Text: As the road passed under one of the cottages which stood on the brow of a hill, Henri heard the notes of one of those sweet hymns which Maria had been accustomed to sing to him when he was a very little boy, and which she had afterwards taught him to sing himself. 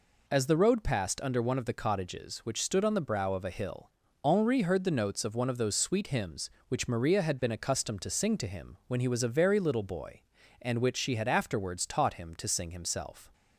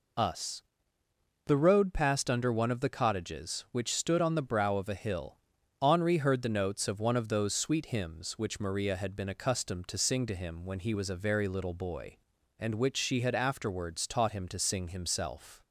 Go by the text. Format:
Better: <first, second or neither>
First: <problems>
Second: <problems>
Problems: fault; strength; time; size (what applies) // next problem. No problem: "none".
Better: first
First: none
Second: says "Us" for "As"; at 0.1 s